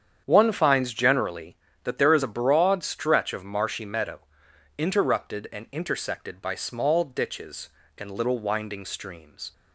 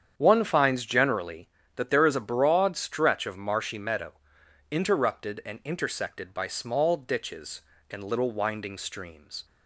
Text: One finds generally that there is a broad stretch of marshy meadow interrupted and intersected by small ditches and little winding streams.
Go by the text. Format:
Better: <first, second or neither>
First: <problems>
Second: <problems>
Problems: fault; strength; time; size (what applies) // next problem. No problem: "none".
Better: neither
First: starts louder than the rest; strong; until 1.2 s; 8.5 dB // pauses between "meadow" and "interrupted"; noticeable; at 4.2 s; 0.56 s long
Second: starts louder than the rest; strong; until 1.1 s; 8.5 dB // pauses between "meadow" and "interrupted"; noticeable; at 4.1 s; 0.56 s long